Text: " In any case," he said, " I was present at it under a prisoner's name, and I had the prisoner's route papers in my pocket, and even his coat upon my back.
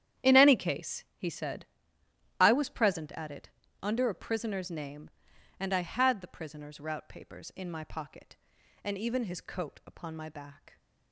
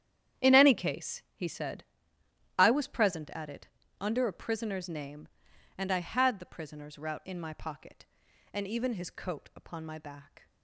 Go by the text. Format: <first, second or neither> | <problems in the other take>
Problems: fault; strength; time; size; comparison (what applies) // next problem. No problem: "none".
first | starts louder than the rest; strong; until 1.4 s; 9.5 dB; strong in the first // pauses between "it" and "under"; slight; at 3.6 s; 0.34 s long; slight in the first // skips "papers"; at 7.2 s